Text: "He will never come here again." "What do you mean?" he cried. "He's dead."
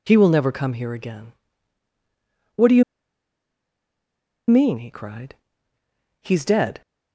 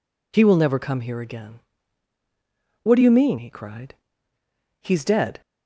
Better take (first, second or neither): second